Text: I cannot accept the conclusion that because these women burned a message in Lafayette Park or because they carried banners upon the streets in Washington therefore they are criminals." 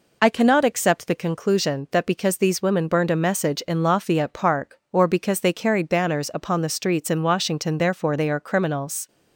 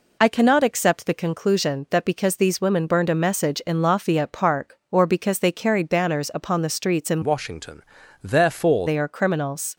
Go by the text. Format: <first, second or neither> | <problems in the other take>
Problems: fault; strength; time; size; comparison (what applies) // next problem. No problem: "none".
first | changes voice from "Washington" to "therefore"; from 7.2 to 8.8 s; 1.6 s long // pauses between "Washington" and "therefore"; at 7.8 s; 0.40 s long